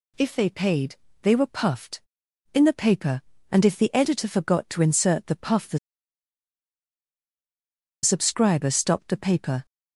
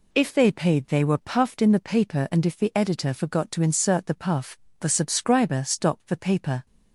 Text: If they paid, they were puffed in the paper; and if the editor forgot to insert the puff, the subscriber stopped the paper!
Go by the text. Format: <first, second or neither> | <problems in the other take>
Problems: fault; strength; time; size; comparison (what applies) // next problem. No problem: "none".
second | pauses between "the" and "subscriber"; strong; at 5.7 s; 2.2 s long